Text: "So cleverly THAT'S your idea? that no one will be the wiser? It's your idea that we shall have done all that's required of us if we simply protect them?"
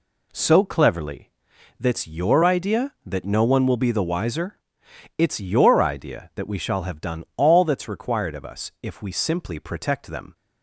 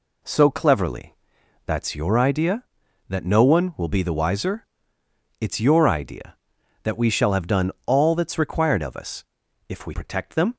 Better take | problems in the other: first | pauses between "cleverly" and "THAT'S"; noticeable; at 1.1 s; 0.50 s long; noticeable in the first // pauses between "done" and "all"; slight; at 7.6 s; 0.16 s long // pauses between "us" and "if"; at 9.2 s; 0.44 s long // skips "simply"; at 9.9 s

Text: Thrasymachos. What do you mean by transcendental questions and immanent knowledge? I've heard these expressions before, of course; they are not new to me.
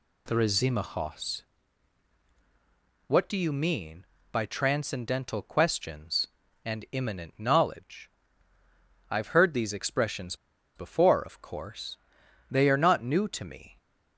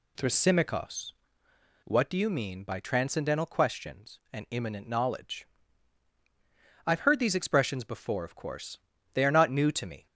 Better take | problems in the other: second | pauses between "expressions" and "before"; at 10.3 s; 0.40 s long

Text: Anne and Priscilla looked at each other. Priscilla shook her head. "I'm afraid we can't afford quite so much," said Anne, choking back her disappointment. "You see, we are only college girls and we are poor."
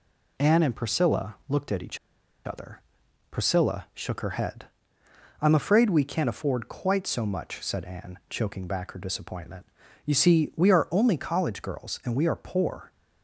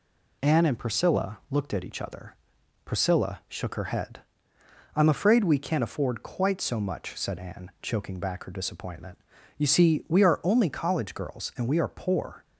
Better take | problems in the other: second | pauses between "each" and "other"; noticeable; at 1.9 s; 0.48 s long

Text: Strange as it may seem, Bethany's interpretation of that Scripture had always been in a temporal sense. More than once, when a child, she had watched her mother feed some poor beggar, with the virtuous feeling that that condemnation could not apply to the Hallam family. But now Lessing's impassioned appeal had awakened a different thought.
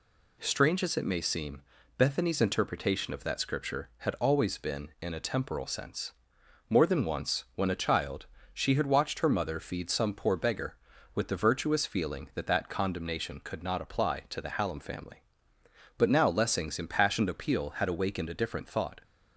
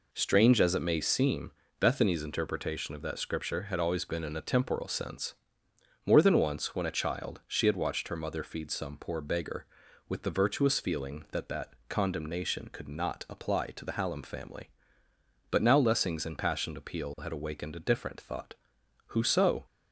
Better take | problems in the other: first | pauses between "that" and "condemnation"; slight; at 11.7 s; 0.16 s long // goes on to say "Who so"; from 19.0 s on; 0.58 s long

